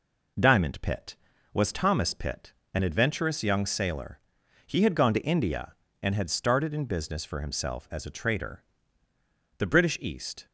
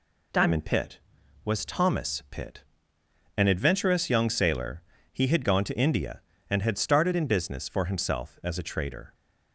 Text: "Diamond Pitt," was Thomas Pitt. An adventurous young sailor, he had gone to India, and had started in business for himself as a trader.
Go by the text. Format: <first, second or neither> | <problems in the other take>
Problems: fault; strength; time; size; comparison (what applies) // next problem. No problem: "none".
second | goes on to say "The British East"; noticeable; from 9.5 s on; 0.88 s long